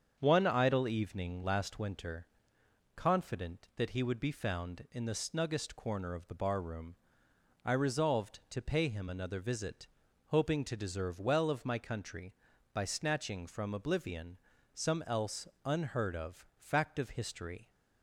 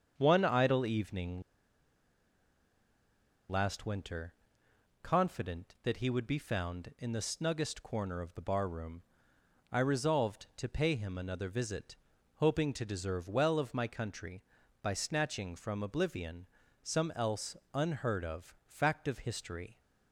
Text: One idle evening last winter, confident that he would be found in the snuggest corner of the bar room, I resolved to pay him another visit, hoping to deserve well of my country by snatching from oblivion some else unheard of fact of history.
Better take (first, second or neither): first